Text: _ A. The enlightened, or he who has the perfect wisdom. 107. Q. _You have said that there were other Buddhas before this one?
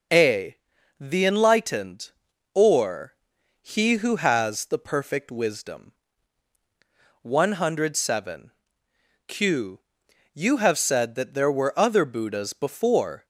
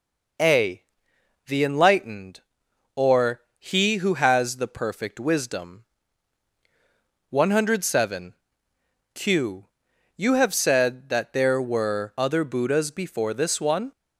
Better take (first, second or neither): second